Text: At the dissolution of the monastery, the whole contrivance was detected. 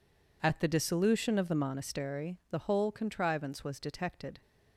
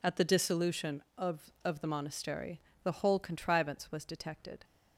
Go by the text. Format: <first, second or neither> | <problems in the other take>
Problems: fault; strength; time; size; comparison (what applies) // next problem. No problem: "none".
first | says "of" twice; at 1.6 s